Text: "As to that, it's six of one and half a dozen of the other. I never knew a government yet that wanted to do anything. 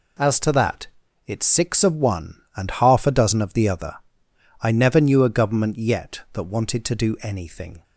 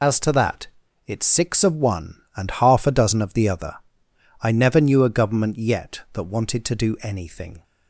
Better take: first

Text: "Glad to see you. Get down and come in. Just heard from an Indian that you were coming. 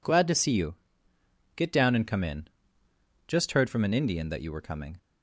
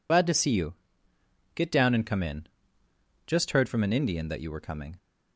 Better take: first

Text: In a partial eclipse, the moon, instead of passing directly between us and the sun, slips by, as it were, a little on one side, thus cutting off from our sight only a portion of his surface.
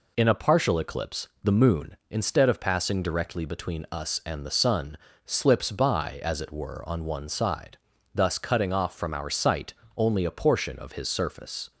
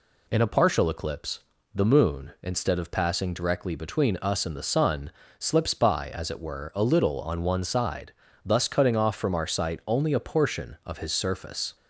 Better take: second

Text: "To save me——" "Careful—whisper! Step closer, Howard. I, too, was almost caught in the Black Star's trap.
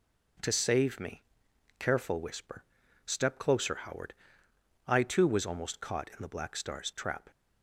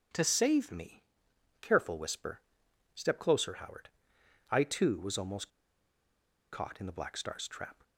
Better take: first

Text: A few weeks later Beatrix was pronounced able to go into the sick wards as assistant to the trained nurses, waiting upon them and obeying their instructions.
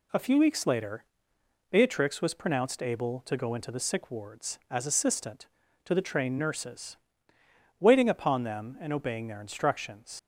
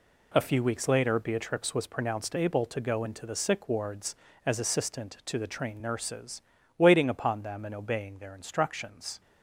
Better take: second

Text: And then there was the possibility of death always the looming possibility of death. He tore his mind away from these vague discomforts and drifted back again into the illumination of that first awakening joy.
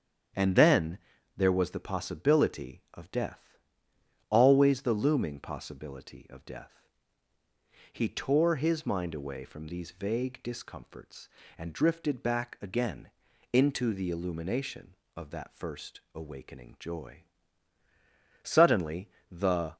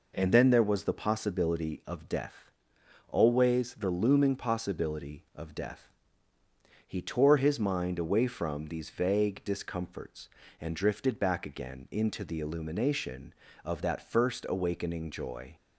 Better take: second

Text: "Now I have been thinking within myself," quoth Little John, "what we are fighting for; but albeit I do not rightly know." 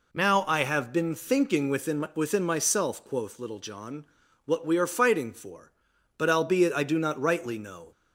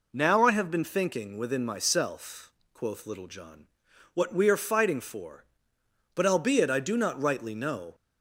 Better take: second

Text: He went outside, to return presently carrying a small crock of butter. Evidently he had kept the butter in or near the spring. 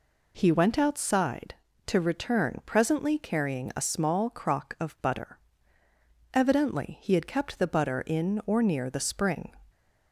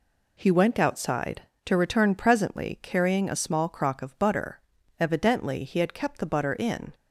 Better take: first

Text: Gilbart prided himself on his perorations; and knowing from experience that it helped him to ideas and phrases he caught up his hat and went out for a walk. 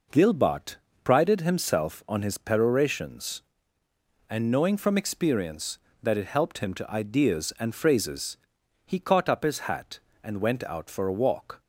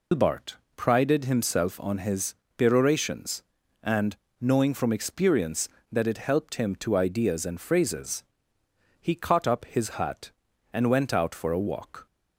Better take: first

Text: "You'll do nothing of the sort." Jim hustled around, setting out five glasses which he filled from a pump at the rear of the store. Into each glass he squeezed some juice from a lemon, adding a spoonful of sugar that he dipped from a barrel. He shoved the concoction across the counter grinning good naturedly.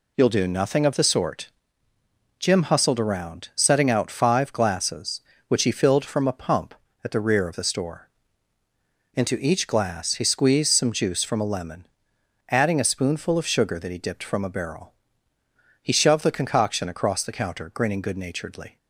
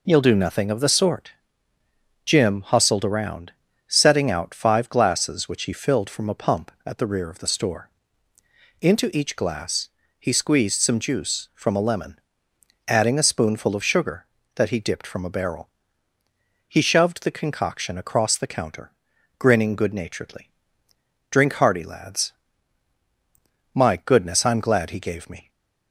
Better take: first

